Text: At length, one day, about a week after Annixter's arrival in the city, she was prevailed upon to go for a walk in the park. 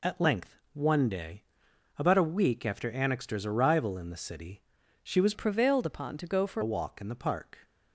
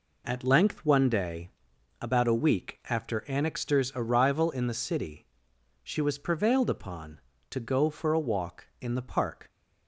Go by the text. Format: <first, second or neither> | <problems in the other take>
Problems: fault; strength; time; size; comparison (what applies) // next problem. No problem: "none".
second | changes voice from "prevailed" to "for"; from 5.3 to 6.6 s; 1.3 s long